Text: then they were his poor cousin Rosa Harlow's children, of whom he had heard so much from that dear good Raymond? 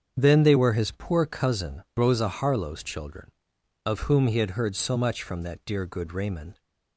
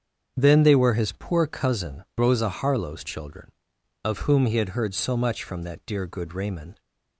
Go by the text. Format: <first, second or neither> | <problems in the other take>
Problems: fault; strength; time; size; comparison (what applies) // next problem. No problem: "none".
neither | starts louder than the rest; strong; the same in both // pauses between "cousin" and "Rosa"; slight; the same in both